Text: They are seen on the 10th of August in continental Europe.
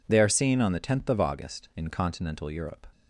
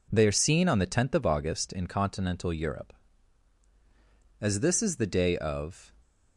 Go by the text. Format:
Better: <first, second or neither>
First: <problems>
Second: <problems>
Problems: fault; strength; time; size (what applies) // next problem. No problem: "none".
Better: first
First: none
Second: goes on to say "As this is the day of"; from 4.4 s on; 1.5 s long